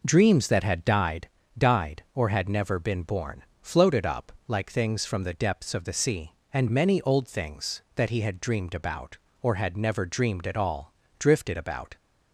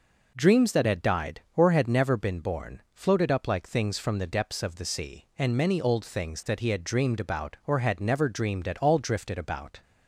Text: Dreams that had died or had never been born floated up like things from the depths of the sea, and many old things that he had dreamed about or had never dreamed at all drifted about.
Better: second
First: says "died" twice; at 1.5 s // pauses between "born" and "floated"; slight; at 3.4 s; 0.16 s long // pauses between "up" and "like"; slight; at 4.3 s; 0.16 s long // pauses between "all" and "drifted"; slight; at 10.9 s; 0.28 s long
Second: none

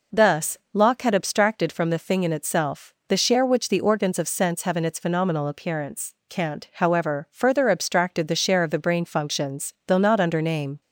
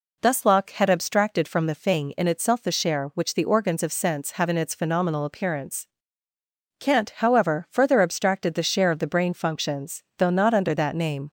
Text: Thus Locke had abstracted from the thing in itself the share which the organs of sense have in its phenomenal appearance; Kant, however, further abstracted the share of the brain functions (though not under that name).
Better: second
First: pauses between "Thus" and "Locke"; slight; at 0.5 s; 0.16 s long // pauses between "itself" and "the"; slight; at 2.9 s; 0.16 s long // skips "that"; at 10.4 s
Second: none

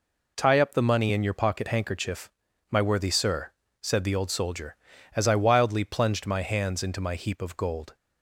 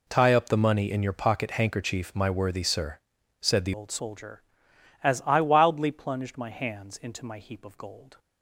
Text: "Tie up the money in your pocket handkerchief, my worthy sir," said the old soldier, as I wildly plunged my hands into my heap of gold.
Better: first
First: none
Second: changes voice at "old"; from 3.7 s on; 4.4 s long

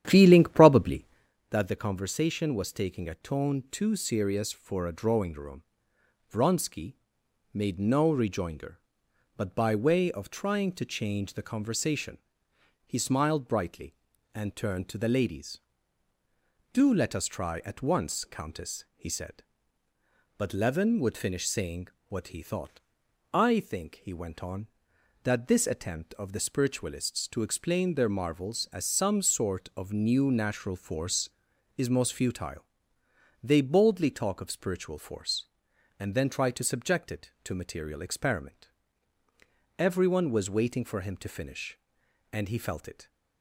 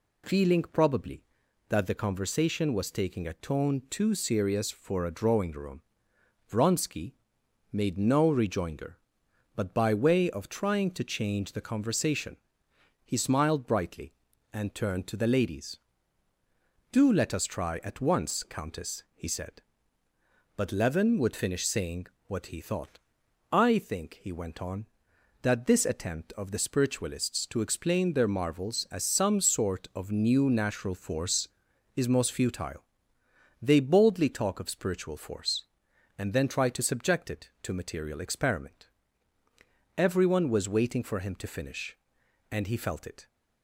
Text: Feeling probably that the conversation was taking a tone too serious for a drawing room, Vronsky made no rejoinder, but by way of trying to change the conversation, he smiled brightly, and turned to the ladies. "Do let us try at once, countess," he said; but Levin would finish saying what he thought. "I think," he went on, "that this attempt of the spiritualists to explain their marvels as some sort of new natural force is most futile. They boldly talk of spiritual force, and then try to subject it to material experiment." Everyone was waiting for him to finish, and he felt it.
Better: second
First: starts louder than the rest; strong; until 1.4 s; 11 dB // pauses between "Vronsky" and "made"; noticeable; at 6.9 s; 0.58 s long // pauses between "saying" and "what"; slight; at 21.8 s; 0.22 s long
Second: pauses between "Vronsky" and "made"; noticeable; at 7.1 s; 0.58 s long // pauses between "saying" and "what"; slight; at 22.0 s; 0.22 s long

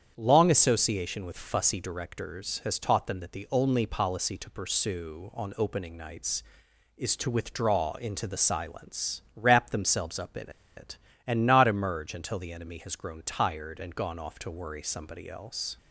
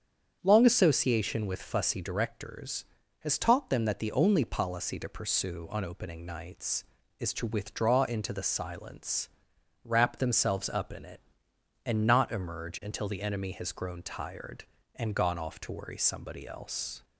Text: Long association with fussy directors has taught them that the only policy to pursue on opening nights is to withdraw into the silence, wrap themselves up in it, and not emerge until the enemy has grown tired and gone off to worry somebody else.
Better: second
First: starts louder than the rest; strong; until 1.1 s; 8.5 dB // pauses between "in" and "it"; slight; at 10.5 s; 0.25 s long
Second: starts louder than the rest; strong; until 1.4 s; 7.5 dB

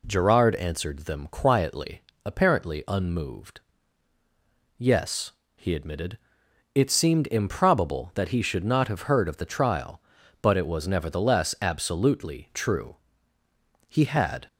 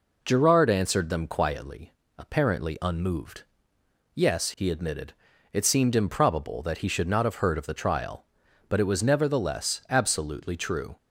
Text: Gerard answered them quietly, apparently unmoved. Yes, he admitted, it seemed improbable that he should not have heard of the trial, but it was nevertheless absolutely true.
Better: second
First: goes on to say "He had"; from 13.8 s on; 0.58 s long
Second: none

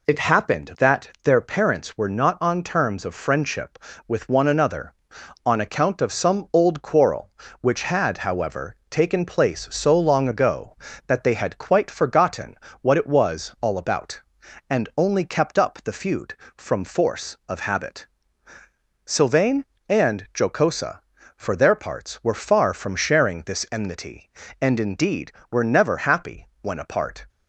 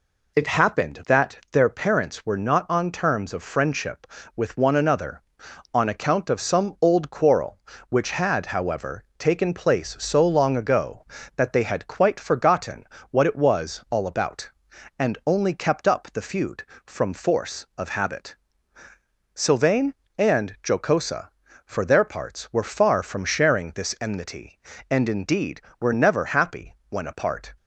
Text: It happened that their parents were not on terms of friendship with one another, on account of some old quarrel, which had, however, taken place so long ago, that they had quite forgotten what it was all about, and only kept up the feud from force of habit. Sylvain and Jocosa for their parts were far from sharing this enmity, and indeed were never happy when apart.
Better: neither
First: pauses between "forgotten" and "what"; slight; at 12.5 s; 0.28 s long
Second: pauses between "forgotten" and "what"; slight; at 12.8 s; 0.28 s long

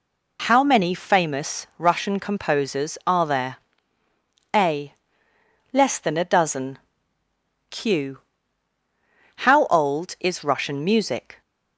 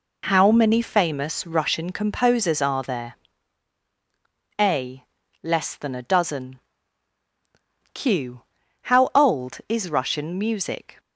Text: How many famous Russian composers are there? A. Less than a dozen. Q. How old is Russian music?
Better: neither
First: none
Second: none

